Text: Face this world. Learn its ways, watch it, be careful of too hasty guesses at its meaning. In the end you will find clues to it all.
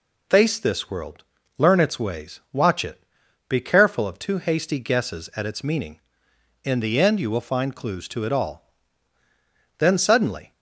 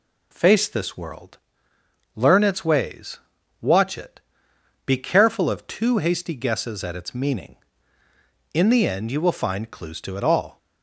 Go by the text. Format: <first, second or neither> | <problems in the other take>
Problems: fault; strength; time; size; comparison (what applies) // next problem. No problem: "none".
second | goes on to say "Then suddenly"; noticeable; from 9.7 s on; 0.74 s long